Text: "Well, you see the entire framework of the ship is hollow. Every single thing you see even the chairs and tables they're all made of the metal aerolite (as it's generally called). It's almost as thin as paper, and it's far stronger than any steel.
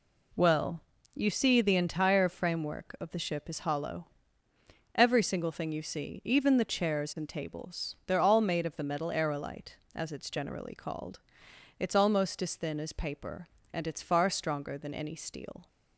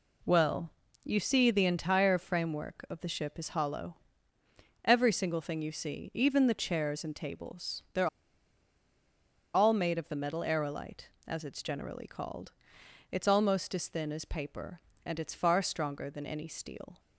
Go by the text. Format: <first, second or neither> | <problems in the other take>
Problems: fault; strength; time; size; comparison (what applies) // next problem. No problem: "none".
first | pauses between "they're" and "all"; strong; at 8.0 s; 1.4 s long